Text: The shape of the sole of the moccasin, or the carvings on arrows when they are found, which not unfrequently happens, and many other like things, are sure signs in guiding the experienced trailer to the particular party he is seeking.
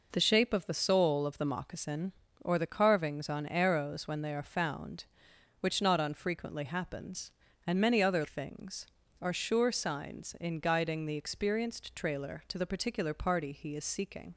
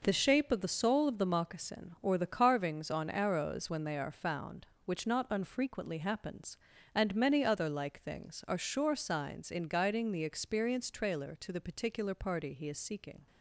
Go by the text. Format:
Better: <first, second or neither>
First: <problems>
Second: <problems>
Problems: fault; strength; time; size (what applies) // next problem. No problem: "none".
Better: second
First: skips "like"; at 8.2 s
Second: none